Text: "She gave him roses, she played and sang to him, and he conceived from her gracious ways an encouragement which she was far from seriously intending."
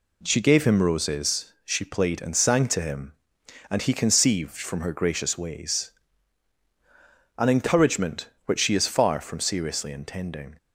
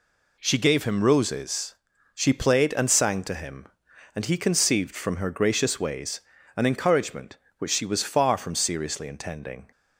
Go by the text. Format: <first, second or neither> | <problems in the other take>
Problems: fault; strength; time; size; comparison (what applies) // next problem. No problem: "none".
second | pauses between "ways" and "an"; strong; at 5.9 s; 1.4 s long; slight in the second // says "is" for "was"; at 8.7 s